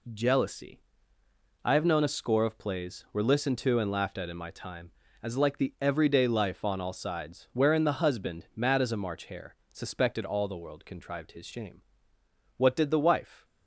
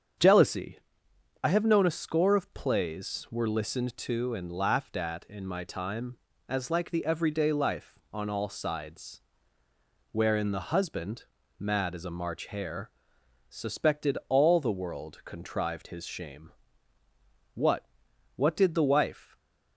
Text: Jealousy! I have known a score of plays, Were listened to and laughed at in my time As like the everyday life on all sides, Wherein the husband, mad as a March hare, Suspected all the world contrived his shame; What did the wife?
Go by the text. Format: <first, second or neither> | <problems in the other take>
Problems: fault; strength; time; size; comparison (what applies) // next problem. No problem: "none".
first | starts louder than the rest; strong; until 1.8 s; 7.5 dB // says "What" twice; at 18.3 s // stays silent after the last word; slight; from 19.2 s on; 0.5 s long